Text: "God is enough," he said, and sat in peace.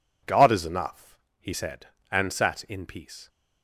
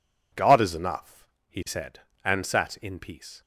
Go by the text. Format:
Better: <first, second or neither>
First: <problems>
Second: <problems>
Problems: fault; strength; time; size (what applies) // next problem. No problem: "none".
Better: neither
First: none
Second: none